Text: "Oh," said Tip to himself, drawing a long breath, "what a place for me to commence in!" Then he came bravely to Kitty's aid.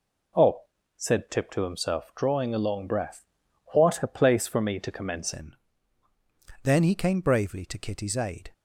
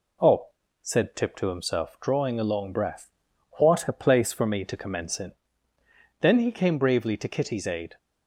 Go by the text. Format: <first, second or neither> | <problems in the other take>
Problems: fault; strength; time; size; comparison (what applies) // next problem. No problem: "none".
second | changes voice at "in"; from 5.3 s on; 3.2 s long